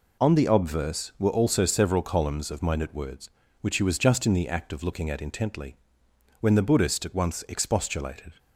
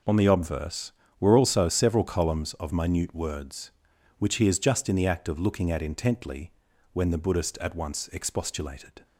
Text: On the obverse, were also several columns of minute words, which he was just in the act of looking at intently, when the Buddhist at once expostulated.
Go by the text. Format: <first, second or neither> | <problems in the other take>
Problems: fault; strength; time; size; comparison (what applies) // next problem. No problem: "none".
first | says "is" for "was"; at 4.4 s